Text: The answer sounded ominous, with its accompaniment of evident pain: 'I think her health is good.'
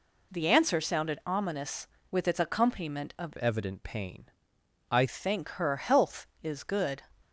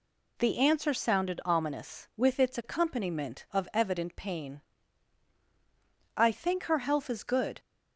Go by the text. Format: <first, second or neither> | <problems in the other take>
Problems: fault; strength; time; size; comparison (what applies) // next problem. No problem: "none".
second | changes voice from "evident" to "I"; from 3.3 to 5.0 s; 1.7 s long